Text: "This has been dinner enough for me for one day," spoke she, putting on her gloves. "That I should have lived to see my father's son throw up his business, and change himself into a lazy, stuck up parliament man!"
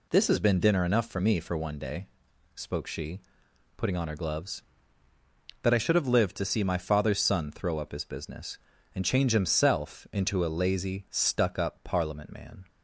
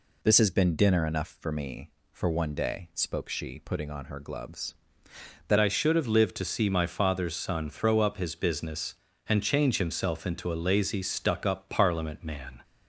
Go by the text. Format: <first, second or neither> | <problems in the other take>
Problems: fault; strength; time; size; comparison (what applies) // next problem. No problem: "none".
first | changes voice at "I"; from 5.5 s on; 7.1 s long